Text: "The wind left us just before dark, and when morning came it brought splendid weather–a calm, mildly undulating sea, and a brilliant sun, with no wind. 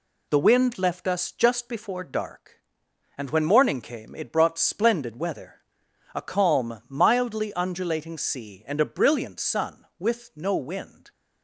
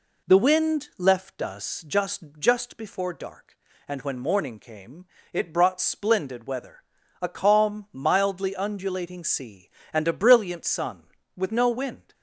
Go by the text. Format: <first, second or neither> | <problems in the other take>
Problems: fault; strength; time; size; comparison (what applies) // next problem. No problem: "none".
first | says "just" twice; at 2.3 s // pauses between "came" and "it"; slight; at 5.0 s; 0.28 s long